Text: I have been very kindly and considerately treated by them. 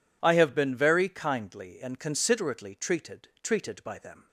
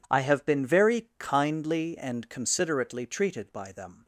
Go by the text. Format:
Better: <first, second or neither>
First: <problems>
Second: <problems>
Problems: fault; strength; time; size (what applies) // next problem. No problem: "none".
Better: second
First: says "treated" twice; at 3.4 s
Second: none